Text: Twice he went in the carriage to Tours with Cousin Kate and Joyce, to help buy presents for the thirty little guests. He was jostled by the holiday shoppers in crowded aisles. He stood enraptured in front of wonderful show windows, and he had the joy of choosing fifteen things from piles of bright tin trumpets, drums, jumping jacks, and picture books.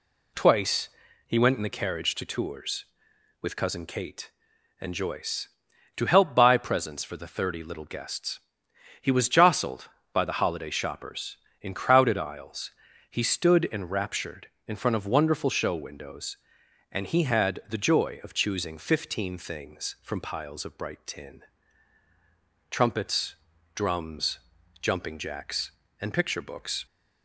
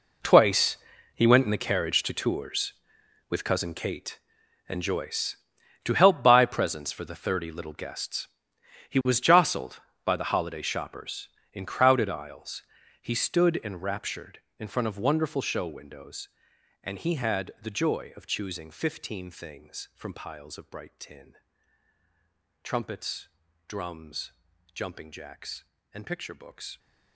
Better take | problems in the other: first | gets quieter; strong; throughout; 15 dB // pauses between "Twice" and "he"; at 0.7 s; 0.38 s long; also in the first // pauses between "tin" and "trumpets"; strong; at 21.3 s; 1.2 s long; strong in the first

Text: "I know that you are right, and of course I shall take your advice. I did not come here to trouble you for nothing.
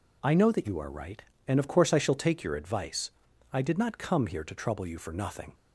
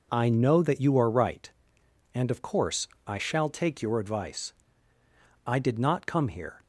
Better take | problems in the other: first | pauses between "course" and "I"; slight; at 2.8 s; 0.18 s long // stops before "to trouble you for nothing"; at 6.6 s

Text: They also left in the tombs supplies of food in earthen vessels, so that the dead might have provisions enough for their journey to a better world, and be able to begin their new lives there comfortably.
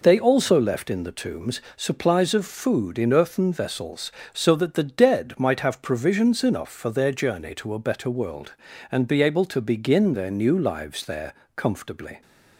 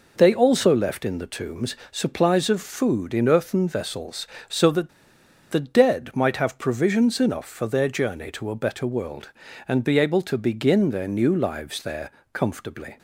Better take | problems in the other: first | pauses between "tombs" and "supplies"; slight; at 1.7 s; 0.16 s long; slight in the first // pauses between "that" and "the"; noticeable; at 4.8 s; 0.61 s long // pauses between "there" and "comfortably"; slight; at 12.1 s; 0.22 s long; slight in the first

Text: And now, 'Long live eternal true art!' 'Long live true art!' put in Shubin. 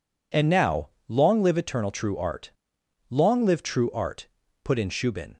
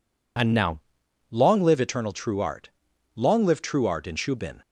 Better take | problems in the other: first | skips "put"; at 4.0 s

